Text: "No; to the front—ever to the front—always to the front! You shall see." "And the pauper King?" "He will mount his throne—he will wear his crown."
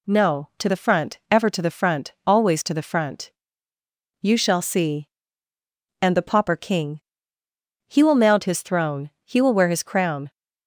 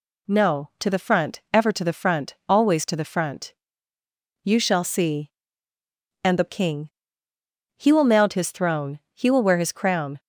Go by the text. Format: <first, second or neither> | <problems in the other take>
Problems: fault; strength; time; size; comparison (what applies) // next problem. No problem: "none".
first | skips "pauper"; at 6.4 s